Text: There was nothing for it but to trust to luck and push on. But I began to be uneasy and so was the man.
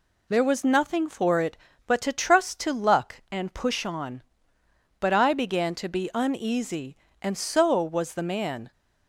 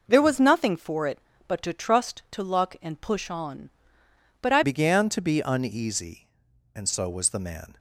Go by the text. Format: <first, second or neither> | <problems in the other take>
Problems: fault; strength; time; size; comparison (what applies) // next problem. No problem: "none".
first | changes voice at "began"; from 4.6 s on; 3.1 s long